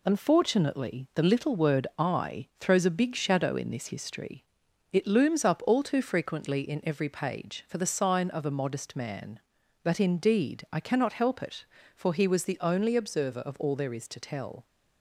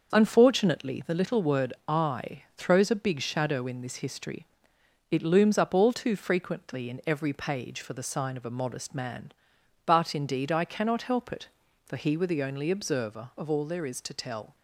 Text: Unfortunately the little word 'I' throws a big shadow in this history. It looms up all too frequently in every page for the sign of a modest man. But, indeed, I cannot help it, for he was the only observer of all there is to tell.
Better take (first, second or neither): first